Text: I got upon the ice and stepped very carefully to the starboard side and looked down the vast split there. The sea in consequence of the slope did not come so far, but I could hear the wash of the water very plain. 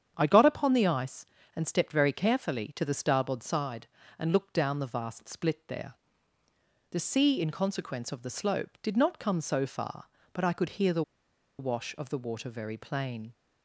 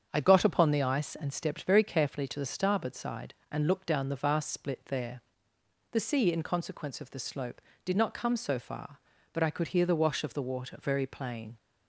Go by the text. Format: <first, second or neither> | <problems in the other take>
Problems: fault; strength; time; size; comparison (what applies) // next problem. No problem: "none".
second | starts louder than the rest; strong; until 1.1 s; 8.5 dB; strong in the second // pauses between "the" and "wash"; noticeable; at 11.0 s; 0.57 s long